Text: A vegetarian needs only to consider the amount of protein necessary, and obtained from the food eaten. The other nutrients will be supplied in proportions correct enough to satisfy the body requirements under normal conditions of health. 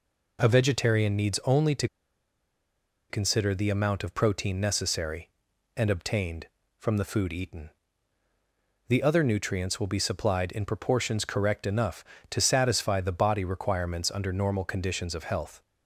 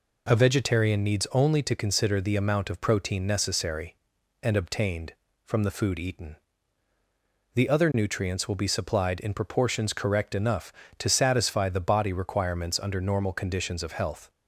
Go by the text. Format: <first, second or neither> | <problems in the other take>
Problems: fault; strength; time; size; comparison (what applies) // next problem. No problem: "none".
second | pauses between "to" and "consider"; at 1.8 s; 1.2 s long